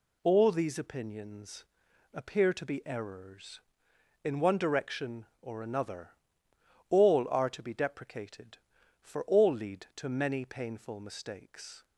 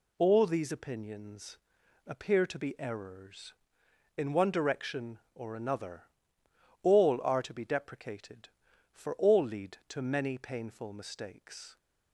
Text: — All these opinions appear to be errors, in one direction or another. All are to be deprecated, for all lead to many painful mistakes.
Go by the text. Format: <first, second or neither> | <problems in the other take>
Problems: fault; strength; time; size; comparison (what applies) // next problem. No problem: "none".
neither | pauses between "opinions" and "appear"; noticeable; the same in both